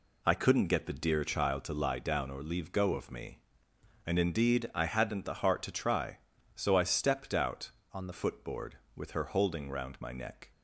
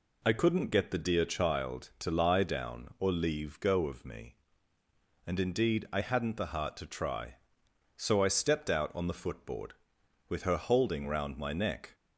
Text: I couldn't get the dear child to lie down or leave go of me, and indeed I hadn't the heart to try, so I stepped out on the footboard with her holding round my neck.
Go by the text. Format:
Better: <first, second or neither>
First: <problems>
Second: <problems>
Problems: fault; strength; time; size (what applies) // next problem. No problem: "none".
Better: second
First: changes voice from "on" to "the"; from 7.9 to 8.1 s; 0.2 s long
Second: none